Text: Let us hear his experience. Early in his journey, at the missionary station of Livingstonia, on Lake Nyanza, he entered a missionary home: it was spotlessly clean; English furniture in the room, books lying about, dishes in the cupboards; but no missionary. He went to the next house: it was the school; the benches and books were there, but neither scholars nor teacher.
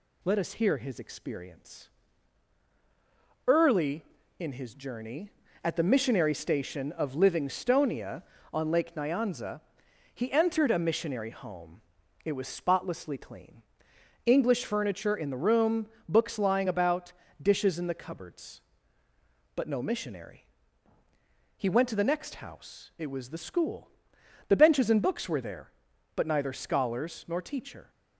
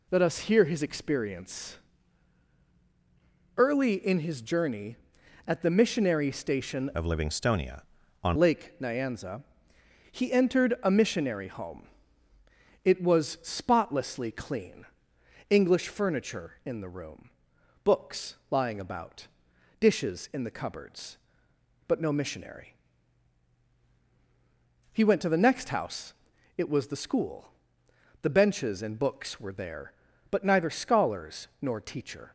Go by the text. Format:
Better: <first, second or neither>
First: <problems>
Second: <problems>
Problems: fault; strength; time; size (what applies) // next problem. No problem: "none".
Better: first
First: none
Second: changes voice from "of" to "on"; from 6.9 to 8.3 s; 1.4 s long // pauses between "scholars" and "nor"; slight; at 31.4 s; 0.16 s long